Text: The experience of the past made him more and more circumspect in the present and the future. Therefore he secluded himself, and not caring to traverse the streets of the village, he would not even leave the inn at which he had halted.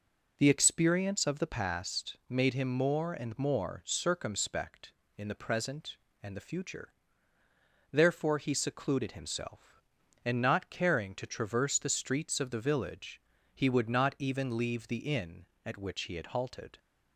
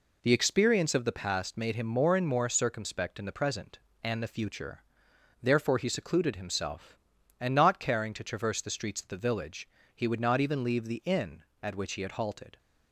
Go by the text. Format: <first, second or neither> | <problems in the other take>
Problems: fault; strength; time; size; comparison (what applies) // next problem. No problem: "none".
neither | none